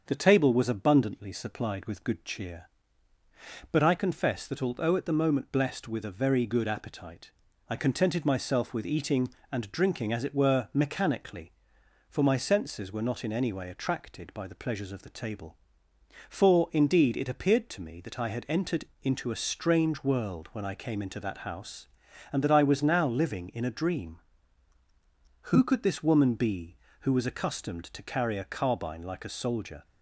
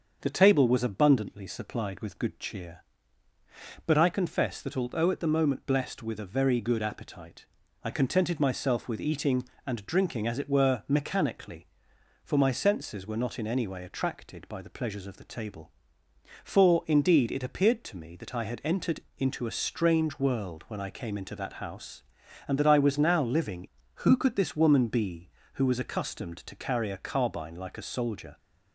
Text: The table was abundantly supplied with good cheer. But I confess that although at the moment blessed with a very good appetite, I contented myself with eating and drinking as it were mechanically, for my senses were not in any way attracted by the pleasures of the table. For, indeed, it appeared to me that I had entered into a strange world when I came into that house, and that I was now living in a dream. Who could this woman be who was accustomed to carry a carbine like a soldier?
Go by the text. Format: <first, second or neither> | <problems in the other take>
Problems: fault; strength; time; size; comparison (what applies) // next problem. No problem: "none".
first | starts louder than the rest; until 1.2 s; 6.5 dB; also in the first // pauses between "entered" and "into"; slight; at 19.0 s; 0.16 s long; slight in the first // skips "in a dream"; at 23.8 s